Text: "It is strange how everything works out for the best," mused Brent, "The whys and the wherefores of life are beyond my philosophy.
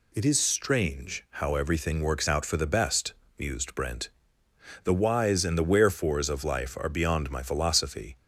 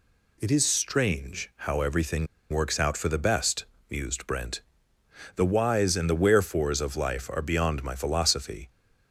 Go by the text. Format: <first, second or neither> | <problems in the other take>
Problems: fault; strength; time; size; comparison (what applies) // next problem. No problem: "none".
first | pauses between "strange" and "how"; slight; at 1.4 s; 0.16 s long; slight in the first // pauses between "everything" and "works"; slight; at 2.2 s; 0.25 s long